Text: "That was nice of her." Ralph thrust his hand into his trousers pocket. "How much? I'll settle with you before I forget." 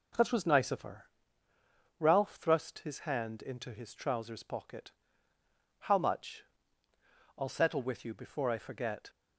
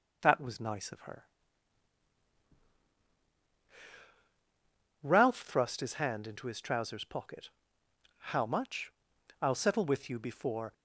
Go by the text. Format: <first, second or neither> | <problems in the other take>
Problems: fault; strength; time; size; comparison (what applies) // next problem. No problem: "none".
first | stops before "I forget"; at 10.7 s